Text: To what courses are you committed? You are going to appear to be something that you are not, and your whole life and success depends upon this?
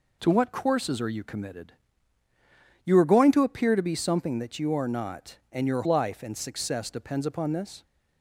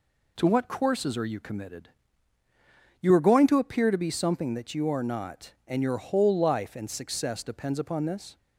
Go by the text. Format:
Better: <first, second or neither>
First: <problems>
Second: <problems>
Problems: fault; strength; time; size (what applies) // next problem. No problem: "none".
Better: second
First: skips "whole"; at 5.8 s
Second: none